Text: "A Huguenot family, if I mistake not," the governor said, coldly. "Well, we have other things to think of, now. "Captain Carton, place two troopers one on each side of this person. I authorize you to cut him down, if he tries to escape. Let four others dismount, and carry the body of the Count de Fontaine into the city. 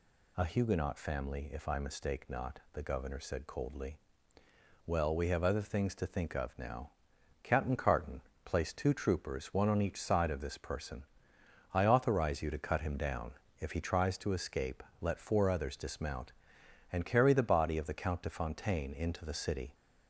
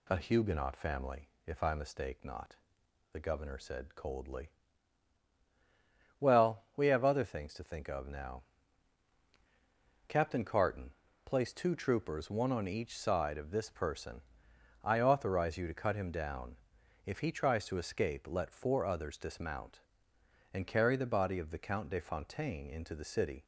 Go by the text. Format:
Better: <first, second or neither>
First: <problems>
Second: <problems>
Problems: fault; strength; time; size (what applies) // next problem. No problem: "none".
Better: neither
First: none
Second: none